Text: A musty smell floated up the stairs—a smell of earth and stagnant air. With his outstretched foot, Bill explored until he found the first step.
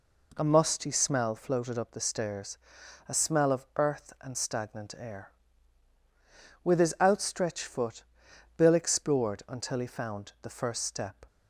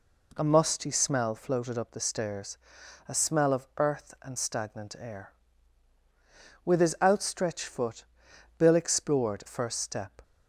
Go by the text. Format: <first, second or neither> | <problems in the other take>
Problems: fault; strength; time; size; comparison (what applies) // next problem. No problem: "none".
first | skips "until he found the"; at 9.4 s